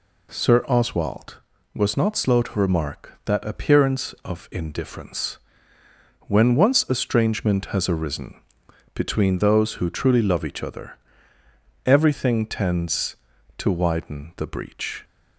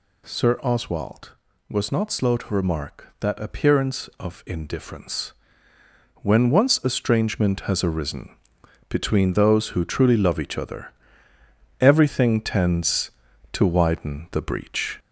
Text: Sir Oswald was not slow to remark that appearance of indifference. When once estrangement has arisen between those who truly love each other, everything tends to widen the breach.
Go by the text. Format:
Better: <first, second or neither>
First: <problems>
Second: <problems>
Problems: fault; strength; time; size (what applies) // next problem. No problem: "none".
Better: first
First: pauses between "arisen" and "between"; noticeable; at 8.3 s; 0.54 s long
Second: gets louder; slight; throughout; 2.5 dB // pauses between "arisen" and "between"; noticeable; at 8.3 s; 0.54 s long